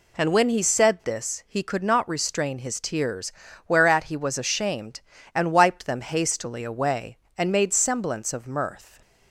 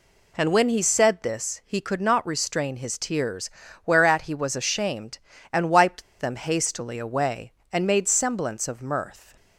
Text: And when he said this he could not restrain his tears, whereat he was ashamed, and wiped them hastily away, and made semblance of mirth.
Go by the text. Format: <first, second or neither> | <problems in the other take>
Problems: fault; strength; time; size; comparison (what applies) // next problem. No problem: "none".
first | pauses between "wiped" and "them"; slight; at 6.0 s; 0.17 s long